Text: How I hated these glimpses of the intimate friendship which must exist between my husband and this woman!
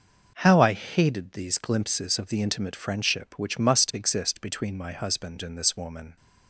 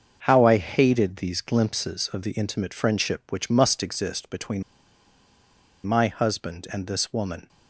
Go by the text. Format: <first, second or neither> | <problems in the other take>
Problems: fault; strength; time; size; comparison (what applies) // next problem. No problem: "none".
first | starts louder than the rest; until 1.2 s; 6.5 dB // pauses between "between" and "my"; at 4.6 s; 1.2 s long